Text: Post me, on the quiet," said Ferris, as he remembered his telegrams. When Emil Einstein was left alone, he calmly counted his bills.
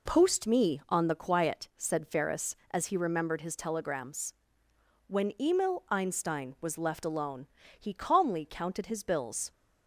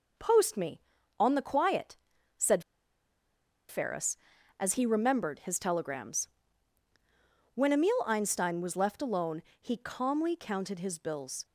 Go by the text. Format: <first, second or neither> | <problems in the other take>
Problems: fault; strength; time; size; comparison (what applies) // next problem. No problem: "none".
first | pauses between "said" and "Ferris"; at 2.6 s; 1.0 s long